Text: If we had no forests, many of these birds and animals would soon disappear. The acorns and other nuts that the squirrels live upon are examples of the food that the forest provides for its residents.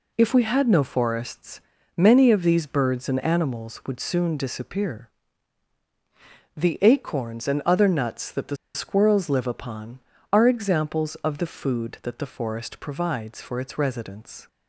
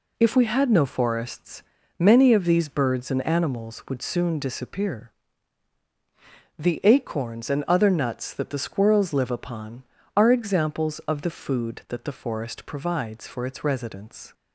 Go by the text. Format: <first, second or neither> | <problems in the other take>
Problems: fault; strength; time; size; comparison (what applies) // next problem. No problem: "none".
second | pauses between "the" and "squirrels"; slight; at 8.5 s; 0.18 s long